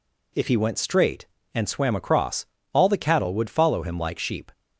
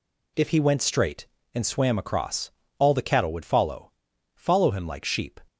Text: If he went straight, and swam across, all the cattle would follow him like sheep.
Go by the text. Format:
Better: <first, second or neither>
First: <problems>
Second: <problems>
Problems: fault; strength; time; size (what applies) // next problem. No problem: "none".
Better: first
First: none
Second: says "follow" twice; at 4.3 s